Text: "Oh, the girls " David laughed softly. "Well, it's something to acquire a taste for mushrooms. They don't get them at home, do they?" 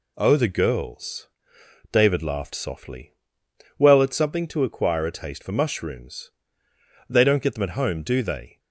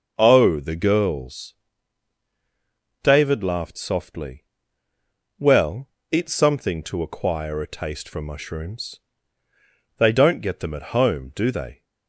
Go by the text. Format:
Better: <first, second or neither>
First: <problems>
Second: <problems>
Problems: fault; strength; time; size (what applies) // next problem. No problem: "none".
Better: neither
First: none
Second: none